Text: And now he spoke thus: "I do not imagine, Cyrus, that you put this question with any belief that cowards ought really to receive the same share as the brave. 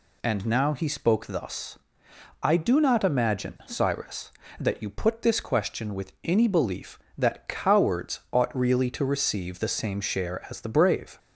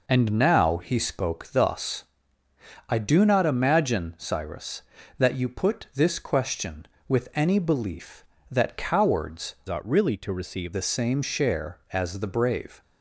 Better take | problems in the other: first | changes voice from "ought" to "receive"; from 9.6 to 10.7 s; 1.1 s long

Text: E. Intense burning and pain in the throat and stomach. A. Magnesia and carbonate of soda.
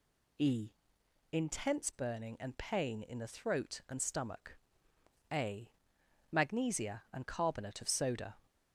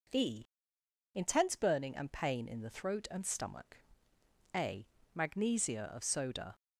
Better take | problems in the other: first | skips "and carbonate"; at 5.9 s

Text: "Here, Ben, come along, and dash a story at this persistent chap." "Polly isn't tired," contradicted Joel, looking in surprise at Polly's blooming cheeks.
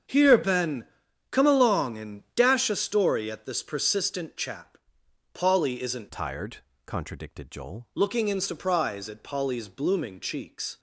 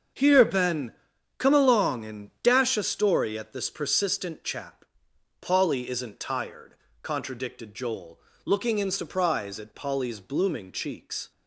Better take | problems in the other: second | starts louder than the rest; strong; until 1.5 s; 7.5 dB; also in the second // changes voice from "tired" to "Joel"; from 6.0 to 7.8 s; 1.8 s long

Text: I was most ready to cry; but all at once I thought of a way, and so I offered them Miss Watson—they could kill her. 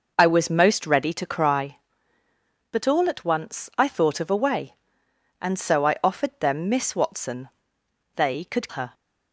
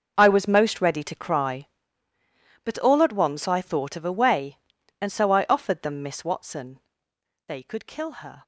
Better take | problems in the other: second | skips "kill"; at 8.6 s

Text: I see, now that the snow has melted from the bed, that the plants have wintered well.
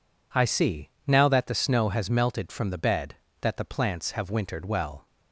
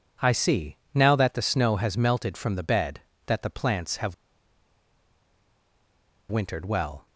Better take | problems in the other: first | pauses between "have" and "wintered"; strong; at 4.1 s; 2.1 s long

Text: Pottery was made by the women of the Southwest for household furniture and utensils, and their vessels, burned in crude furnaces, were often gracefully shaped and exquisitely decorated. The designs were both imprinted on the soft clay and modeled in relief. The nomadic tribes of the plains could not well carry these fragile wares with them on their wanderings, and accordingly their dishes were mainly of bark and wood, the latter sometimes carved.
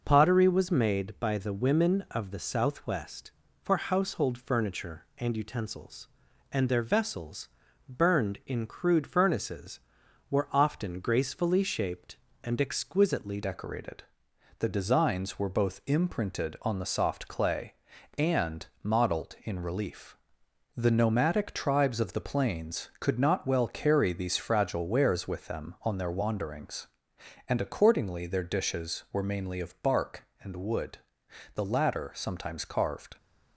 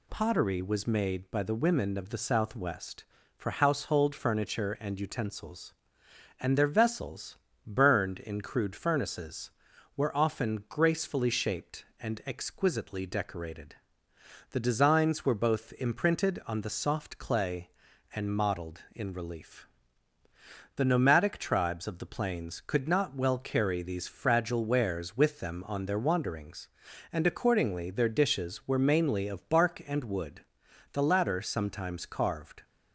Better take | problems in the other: second | changes voice at "decorated"; from 13.4 s on; 19.7 s long // pauses between "and" and "modeled"; slight; at 18.6 s; 0.18 s long

